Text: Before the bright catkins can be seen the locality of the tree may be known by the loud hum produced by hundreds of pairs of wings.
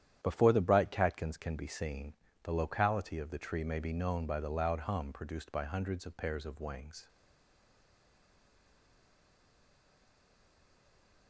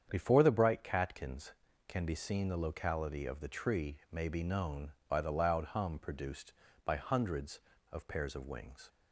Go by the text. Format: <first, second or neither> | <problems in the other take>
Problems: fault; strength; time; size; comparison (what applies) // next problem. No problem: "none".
second | starts louder than the rest; strong; until 1.2 s; 10 dB; strong in the second // pauses between "seen" and "the"; slight; at 2.1 s; 0.30 s long // stays silent after the last word; strong; from 7.0 s on; 4.2 s long